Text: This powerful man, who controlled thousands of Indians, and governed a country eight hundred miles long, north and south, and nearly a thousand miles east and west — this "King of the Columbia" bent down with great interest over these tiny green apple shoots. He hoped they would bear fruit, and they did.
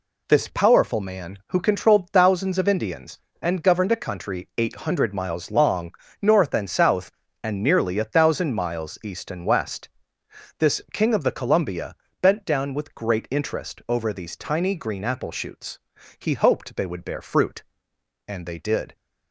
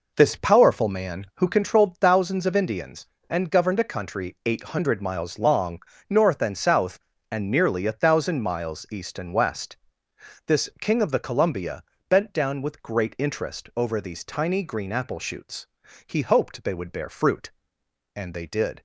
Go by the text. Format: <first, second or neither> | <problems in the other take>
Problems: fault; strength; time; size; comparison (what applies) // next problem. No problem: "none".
first | starts louder than the rest; noticeable; until 1.7 s; 4.5 dB // pauses between "Columbia" and "bent"; slight; at 11.8 s; 0.28 s long; slight in the first